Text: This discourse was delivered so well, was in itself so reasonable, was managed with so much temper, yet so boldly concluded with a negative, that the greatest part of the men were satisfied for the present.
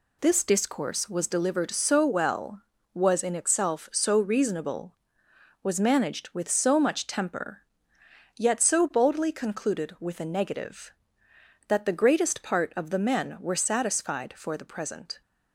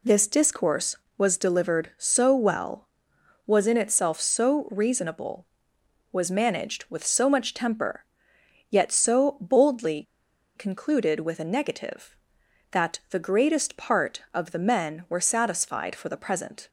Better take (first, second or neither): first